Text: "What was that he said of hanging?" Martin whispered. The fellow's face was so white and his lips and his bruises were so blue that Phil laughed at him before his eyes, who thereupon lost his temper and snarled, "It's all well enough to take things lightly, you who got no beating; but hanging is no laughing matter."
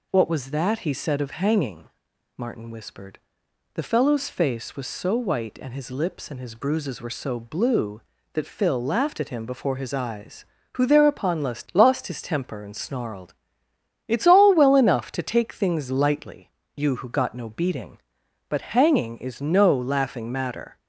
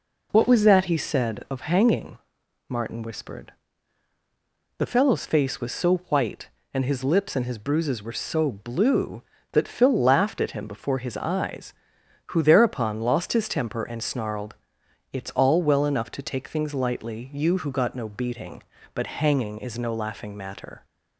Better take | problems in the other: second | says "lost" twice; at 11.7 s

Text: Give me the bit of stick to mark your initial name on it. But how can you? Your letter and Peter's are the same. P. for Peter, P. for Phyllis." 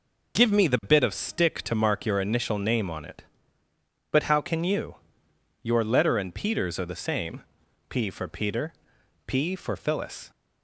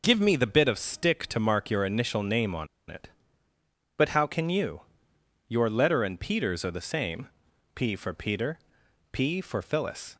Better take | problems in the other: first | pauses between "on" and "it"; slight; at 2.6 s; 0.22 s long

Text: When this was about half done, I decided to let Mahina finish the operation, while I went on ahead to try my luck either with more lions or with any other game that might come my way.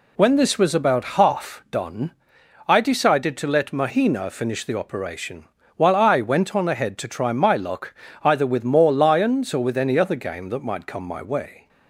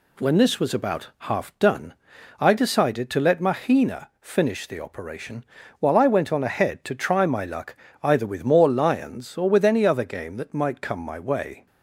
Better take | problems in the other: neither | pauses between "luck" and "either"; slight; the same in both

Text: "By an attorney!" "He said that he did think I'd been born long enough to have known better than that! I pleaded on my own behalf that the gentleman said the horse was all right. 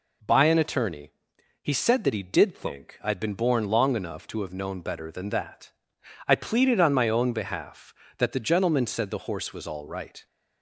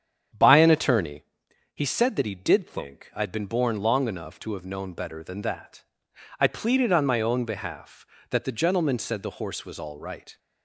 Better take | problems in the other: first | starts louder than the rest; strong; until 1.4 s; 8.5 dB

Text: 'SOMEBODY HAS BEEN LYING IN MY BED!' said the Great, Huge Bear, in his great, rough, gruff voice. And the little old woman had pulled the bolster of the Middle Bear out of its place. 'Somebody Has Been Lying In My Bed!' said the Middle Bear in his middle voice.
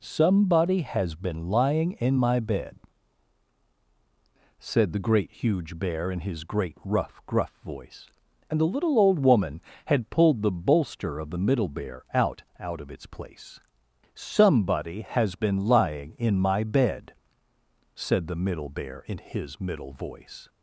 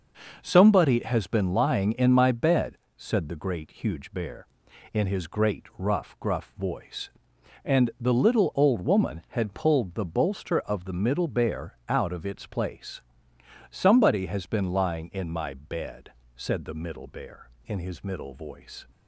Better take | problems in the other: second | says "out" twice; at 12.5 s

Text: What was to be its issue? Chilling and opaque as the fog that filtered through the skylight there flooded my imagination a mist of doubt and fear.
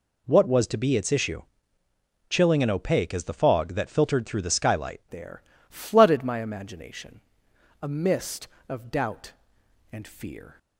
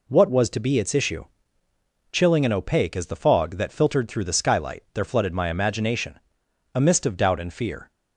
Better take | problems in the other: second | changes voice at "there"; from 5.0 s on; 5.5 s long // pauses between "there" and "flooded"; slight; at 5.4 s; 0.28 s long // pauses between "imagination" and "a"; noticeable; at 7.1 s; 0.62 s long; noticeable in the second

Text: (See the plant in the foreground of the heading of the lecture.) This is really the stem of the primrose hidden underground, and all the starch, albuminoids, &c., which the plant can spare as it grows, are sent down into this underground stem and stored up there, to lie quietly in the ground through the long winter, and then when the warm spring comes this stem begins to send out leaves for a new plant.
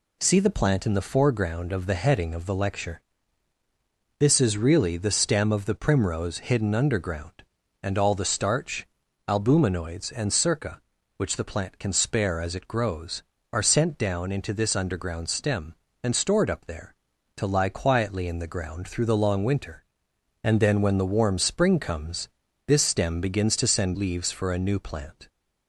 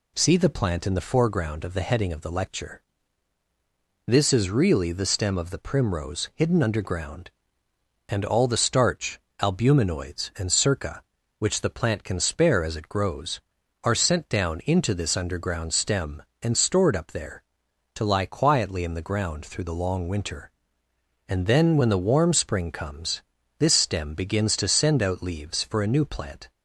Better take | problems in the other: second | pauses between "comes" and "this"; at 22.2 s; 0.38 s long; also in the second // skips "out"; at 23.9 s

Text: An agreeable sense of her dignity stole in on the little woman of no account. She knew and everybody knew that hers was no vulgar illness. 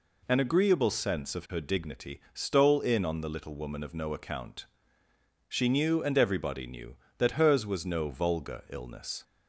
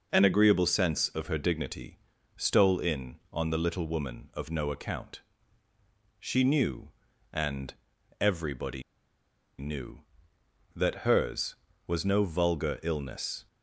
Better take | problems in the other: first | pauses between "dignity" and "stole"; at 1.9 s; 0.38 s long // pauses between "and" and "everybody"; noticeable; at 7.7 s; 0.46 s long // pauses between "everybody" and "knew"; noticeable; at 8.8 s; 0.76 s long

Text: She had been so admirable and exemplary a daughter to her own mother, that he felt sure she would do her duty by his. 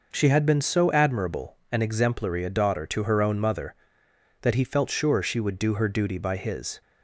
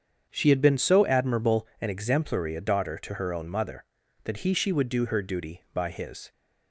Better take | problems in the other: first | starts louder than the rest; strong; until 1.3 s; 7.5 dB // skips "felt sure"; at 4.5 s

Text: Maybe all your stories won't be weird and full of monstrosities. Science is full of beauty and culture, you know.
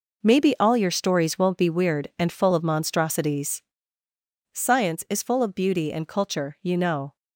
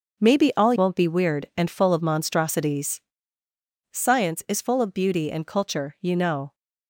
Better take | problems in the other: first | starts louder than the rest; until 1.2 s; 6.5 dB // skips "your stories"; at 0.7 s

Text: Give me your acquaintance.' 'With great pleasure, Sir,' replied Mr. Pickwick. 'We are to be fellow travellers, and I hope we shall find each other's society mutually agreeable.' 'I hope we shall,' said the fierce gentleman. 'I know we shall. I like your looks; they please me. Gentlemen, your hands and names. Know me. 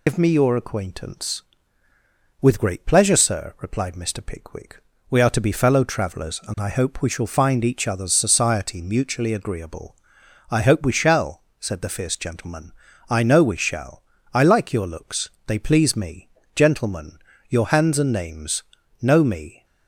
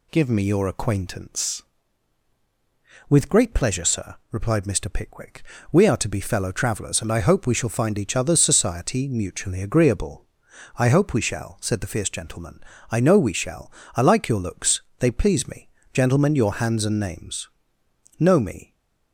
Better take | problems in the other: second | loses the start of "Give"; at 0.0 s; 90 ms

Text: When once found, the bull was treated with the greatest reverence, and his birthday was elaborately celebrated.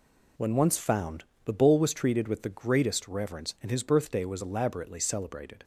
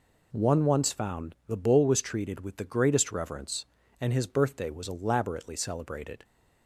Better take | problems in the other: first | says "One" for "When"; at 0.3 s

